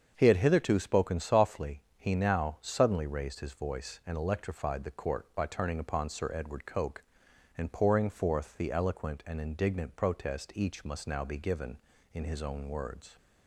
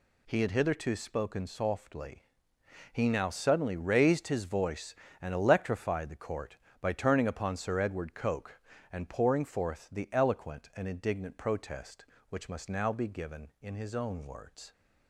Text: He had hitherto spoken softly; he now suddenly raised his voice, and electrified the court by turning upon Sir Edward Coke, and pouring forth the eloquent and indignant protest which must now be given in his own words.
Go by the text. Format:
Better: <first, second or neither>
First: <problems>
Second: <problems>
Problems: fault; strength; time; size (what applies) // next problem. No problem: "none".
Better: second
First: starts louder than the rest; until 1.1 s; 7 dB // says "each" for "which"; at 10.5 s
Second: none